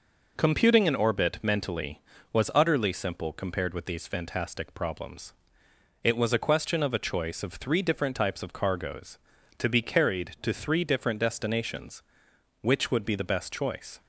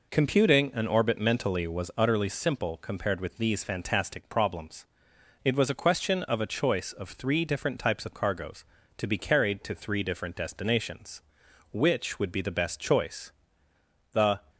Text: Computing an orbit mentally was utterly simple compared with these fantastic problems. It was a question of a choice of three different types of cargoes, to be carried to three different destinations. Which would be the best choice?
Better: first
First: none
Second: goes on to say "The"; slight; from 14.1 s on; 0.26 s long

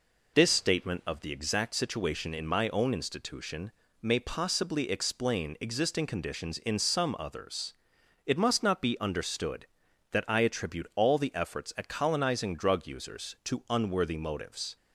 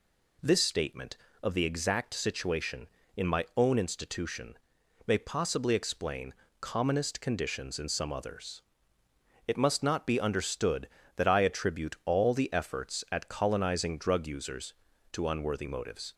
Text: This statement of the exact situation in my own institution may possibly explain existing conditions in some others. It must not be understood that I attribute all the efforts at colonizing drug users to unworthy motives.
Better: first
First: pauses between "institution" and "may"; slight; at 3.7 s; 0.28 s long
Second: pauses between "institution" and "may"; noticeable; at 4.5 s; 0.52 s long // says "commonest" for "existing"; at 6.6 s

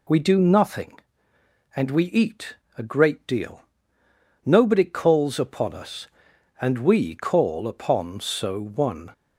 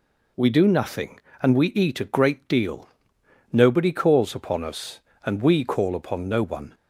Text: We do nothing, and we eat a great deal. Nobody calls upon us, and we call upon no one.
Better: second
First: pauses between "eat" and "a"; slight; at 2.5 s; 0.22 s long // says "so" for "no"; at 8.2 s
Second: none

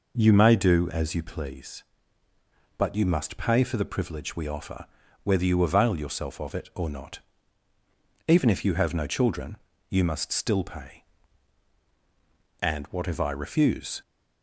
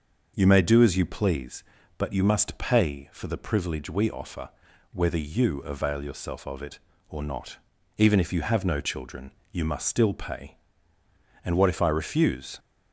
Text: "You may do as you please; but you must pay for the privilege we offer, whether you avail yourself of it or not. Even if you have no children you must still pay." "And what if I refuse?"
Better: neither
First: pauses between "children" and "you"; slight; at 9.5 s; 0.32 s long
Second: pauses between "children" and "you"; slight; at 9.3 s; 0.22 s long

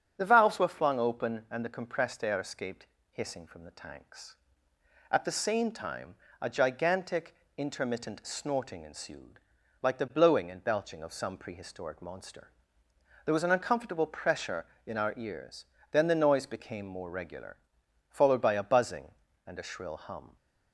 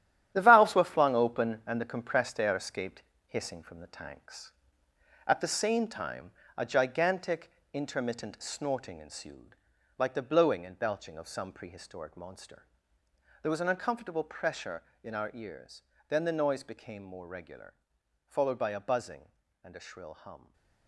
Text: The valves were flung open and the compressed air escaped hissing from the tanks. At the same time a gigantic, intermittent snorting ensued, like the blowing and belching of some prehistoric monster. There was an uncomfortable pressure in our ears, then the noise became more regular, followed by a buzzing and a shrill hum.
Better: first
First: starts louder than the rest; strong; until 1.2 s; 9 dB // pauses between "escaped" and "hissing"; slight; at 2.8 s; 0.24 s long // pauses between "time" and "a"; slight; at 6.1 s; 0.26 s long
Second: gets quieter; strong; throughout; 9 dB // starts louder than the rest; strong; until 1.3 s; 12 dB // pauses between "escaped" and "hissing"; slight; at 3.0 s; 0.24 s long // pauses between "time" and "a"; slight; at 6.3 s; 0.26 s long // stays silent after the last word; slight; from 20.3 s on; 0.5 s long

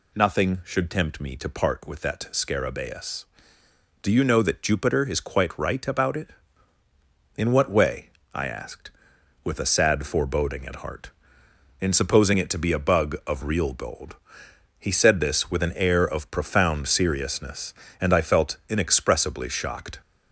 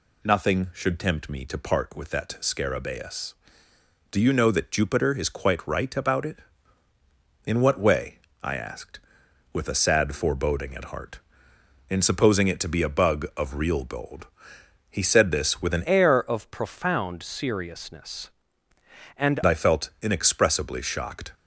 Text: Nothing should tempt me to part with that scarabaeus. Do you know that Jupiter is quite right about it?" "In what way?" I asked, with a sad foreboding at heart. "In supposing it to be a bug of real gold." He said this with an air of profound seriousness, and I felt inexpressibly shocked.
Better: first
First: none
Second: changes voice from "air" to "and"; from 15.8 to 19.3 s; 3.5 s long

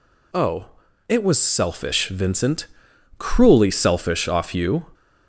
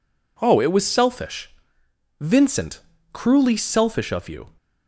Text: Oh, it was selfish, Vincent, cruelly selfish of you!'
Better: second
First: says "off" for "of"; at 4.2 s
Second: none

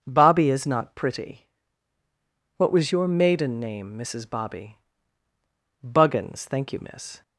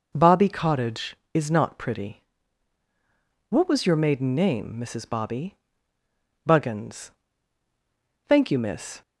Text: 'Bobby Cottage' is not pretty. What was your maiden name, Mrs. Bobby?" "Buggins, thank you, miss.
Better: second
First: starts louder than the rest; until 1.0 s; 6 dB // skips "Cottage"; at 0.4 s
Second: none

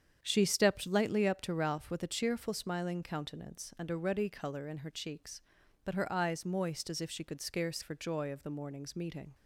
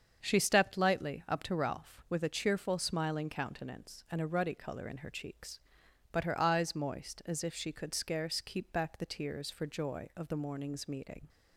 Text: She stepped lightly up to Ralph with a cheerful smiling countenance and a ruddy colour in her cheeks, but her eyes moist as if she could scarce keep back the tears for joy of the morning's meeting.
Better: second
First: starts louder than the rest; strong; until 1.2 s; 8 dB // skips "keep back the tears"; at 7.8 s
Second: starts louder than the rest; strong; until 1.2 s; 7 dB

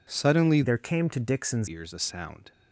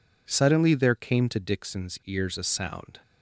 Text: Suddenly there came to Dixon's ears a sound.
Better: second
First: changes voice from "there" to "Dixon's"; from 0.6 to 1.6 s; 1.0 s long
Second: none

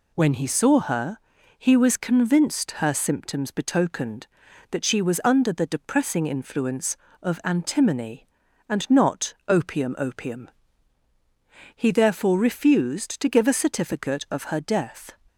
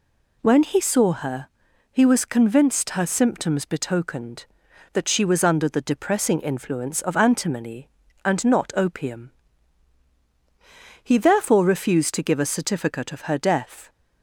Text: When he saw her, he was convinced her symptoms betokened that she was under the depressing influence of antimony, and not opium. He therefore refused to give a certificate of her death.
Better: second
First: pauses between "not" and "opium"; slight; at 9.3 s; 0.16 s long // says "opium" twice; at 9.9 s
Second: none

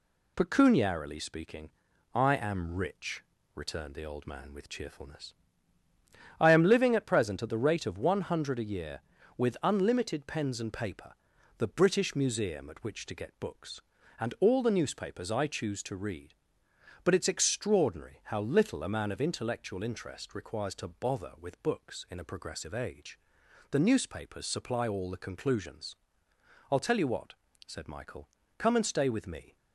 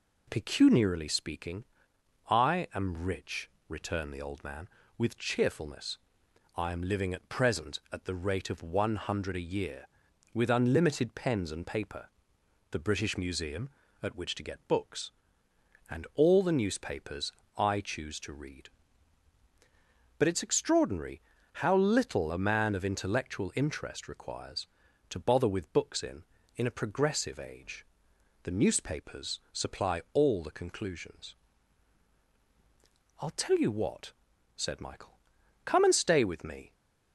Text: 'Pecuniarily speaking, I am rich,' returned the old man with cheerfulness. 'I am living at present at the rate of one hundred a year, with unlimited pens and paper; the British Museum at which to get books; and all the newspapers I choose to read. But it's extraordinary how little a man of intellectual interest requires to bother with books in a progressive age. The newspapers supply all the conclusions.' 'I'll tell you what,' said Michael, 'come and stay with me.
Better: first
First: none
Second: pauses between "newspapers" and "I"; slight; at 17.3 s; 0.24 s long // pauses between "extraordinary" and "how"; slight; at 21.2 s; 0.32 s long // says "in" twice; at 26.5 s

